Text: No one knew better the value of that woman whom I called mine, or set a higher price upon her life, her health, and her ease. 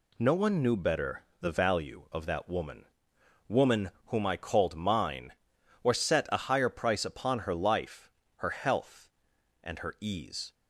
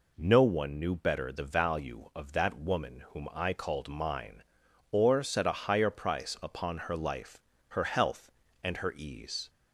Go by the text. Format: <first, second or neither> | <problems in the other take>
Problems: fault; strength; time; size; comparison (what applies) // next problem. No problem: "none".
second | pauses between "better" and "the"; slight; at 1.2 s; 0.16 s long // says "woman" twice; at 3.4 s